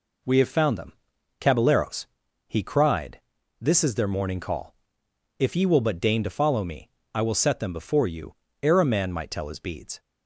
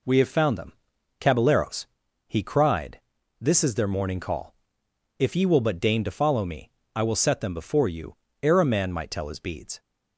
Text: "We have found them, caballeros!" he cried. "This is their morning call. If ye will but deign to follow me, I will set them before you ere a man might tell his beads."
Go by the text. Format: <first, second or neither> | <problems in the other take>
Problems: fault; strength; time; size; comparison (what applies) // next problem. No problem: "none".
neither | pauses between "you" and "ere"; slight; the same in both